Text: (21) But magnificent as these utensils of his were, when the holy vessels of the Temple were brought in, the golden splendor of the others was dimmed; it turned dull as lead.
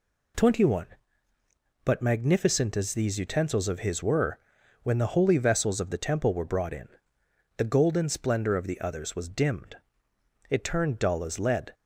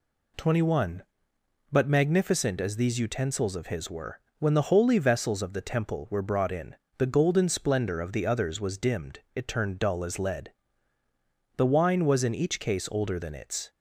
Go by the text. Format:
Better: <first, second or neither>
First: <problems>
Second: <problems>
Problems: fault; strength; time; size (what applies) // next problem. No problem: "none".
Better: first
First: none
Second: goes on to say "The wine was in each case older than its"; strong; from 11.5 s on; 2.1 s long